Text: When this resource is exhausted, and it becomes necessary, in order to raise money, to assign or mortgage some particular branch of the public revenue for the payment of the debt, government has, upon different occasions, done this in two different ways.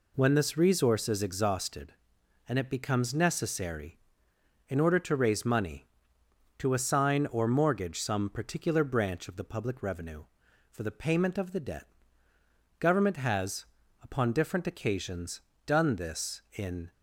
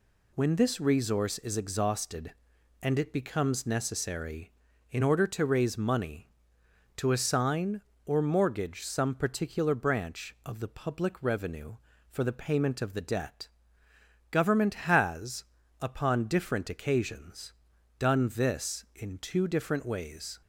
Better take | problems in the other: second | stops before "two different ways"; at 16.9 s

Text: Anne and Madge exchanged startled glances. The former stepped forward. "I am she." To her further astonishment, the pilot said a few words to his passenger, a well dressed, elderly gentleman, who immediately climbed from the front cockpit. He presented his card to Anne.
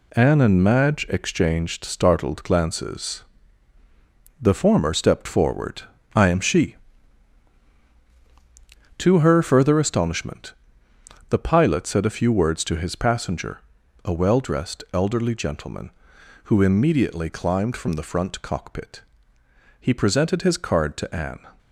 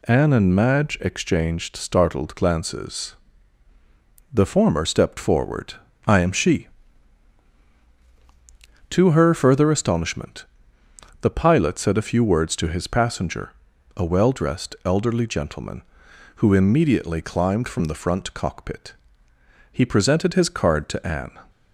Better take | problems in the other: second | gets quieter; throughout; 7 dB

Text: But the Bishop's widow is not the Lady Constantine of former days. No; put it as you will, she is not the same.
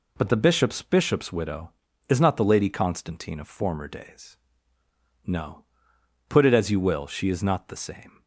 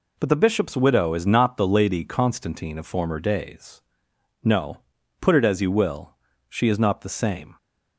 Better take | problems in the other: second | says "Bishop's" twice; at 0.8 s

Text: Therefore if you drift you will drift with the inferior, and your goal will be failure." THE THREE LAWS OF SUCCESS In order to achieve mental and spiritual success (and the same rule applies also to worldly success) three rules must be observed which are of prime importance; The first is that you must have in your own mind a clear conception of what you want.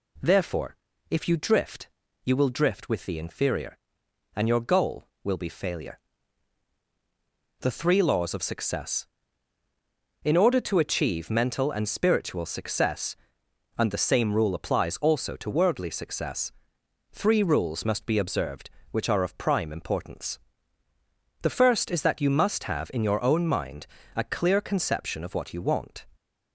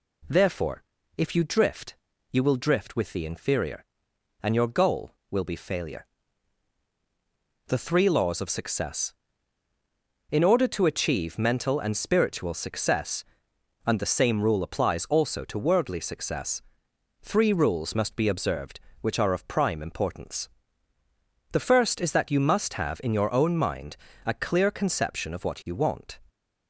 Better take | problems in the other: neither | pauses between "Therefore" and "if"; slight; the same in both // pauses between "drift" and "you"; slight; the same in both // pauses between "mind" and "a"; slight; the same in both

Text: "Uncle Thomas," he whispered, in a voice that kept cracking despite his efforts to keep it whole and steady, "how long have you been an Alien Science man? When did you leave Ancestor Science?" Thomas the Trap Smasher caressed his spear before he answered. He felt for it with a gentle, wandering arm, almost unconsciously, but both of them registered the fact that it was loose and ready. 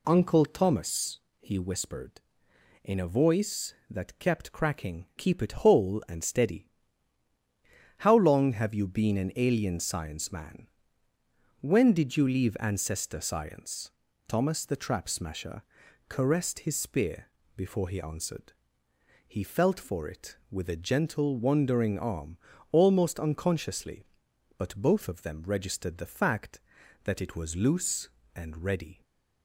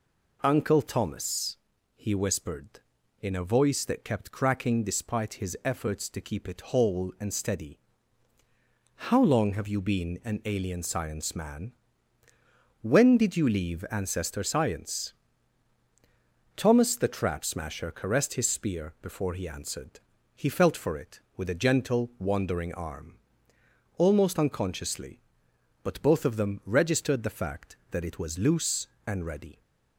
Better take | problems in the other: second | skips "despite his efforts to"; at 5.1 s // pauses between "Smasher" and "caressed"; noticeable; at 15.6 s; 0.46 s long // pauses between "spear" and "before"; slight; at 17.2 s; 0.28 s long // stays silent after the last word; slight; from 28.9 s on; 0.5 s long

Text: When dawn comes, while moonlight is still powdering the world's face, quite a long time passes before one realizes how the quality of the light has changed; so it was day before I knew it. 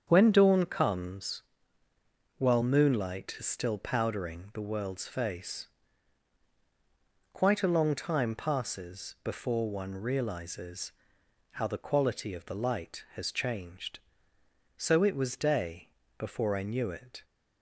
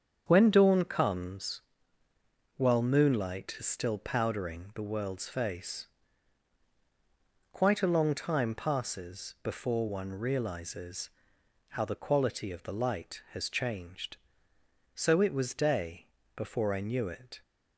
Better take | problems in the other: neither | starts louder than the rest; strong; the same in both // pauses between "realizes" and "how"; noticeable; the same in both // pauses between "day" and "before"; slight; the same in both

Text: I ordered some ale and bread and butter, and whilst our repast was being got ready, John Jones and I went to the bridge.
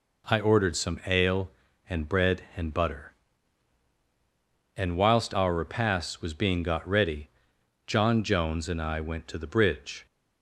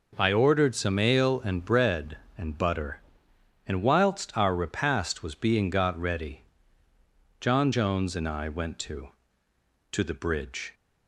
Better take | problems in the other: first | says "to" twice; at 9.9 s

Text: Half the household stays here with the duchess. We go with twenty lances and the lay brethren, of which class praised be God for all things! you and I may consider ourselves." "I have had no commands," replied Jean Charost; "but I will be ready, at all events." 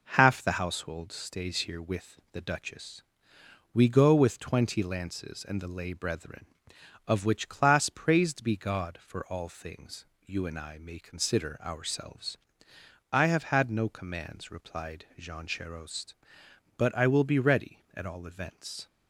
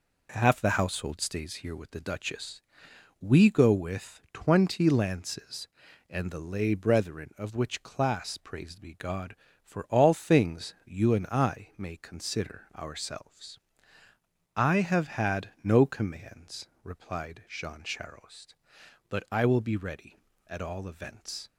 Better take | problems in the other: neither | none

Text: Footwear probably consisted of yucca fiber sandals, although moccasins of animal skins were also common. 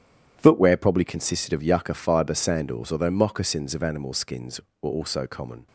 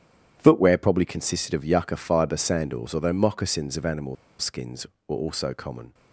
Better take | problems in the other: first | starts louder than the rest; strong; until 1.3 s; 10 dB; strong in the first // pauses between "animal" and "skins"; slight; at 4.1 s; 0.24 s long

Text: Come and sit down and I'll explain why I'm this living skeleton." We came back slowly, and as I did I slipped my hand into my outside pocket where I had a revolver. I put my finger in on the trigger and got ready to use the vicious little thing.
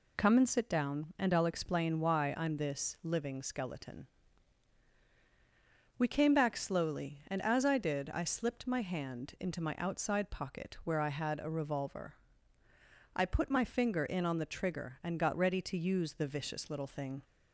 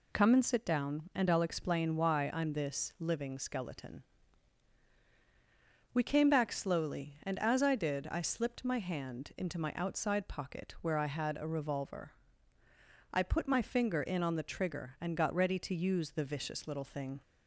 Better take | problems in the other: neither | none

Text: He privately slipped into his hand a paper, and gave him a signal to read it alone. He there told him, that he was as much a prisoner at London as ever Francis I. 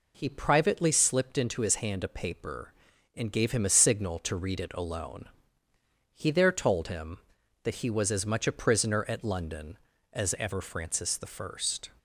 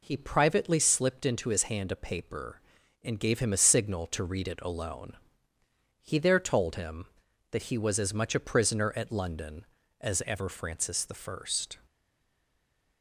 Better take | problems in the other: first | stays silent after the last word; noticeable; from 11.8 s on; 1.2 s long

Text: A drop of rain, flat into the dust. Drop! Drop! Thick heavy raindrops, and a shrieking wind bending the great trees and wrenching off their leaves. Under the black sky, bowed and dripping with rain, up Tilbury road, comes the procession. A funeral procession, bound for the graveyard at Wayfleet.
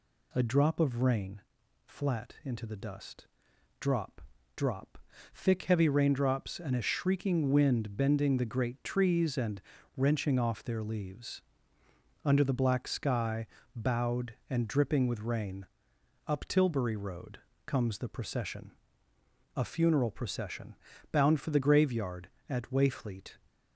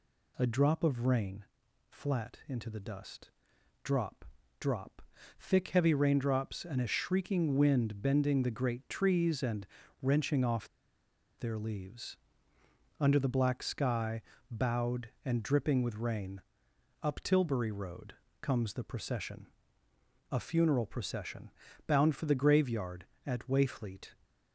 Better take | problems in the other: first | pauses between "and" and "wrenching"; slight; at 9.6 s; 0.36 s long; slight in the first // pauses between "off" and "their"; noticeable; at 10.6 s; 0.70 s long

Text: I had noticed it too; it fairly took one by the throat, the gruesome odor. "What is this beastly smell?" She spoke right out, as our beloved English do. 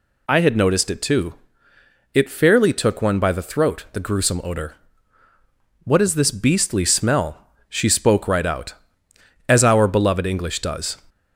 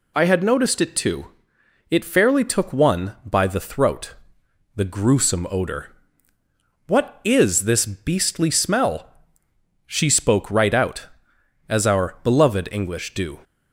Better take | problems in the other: second | says "does" for "do"; at 10.6 s

